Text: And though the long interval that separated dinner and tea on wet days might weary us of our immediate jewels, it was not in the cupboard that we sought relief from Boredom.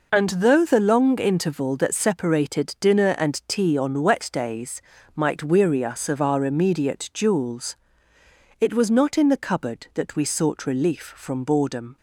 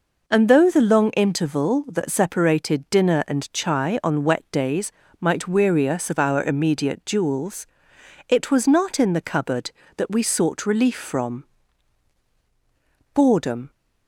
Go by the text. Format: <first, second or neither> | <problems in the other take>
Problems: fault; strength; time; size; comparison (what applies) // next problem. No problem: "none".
first | says "chai" for "tea"; at 3.5 s // pauses between "days" and "might"; slight; at 4.9 s; 0.30 s long; slight in the first // pauses between "from" and "Boredom"; strong; at 11.4 s; 1.7 s long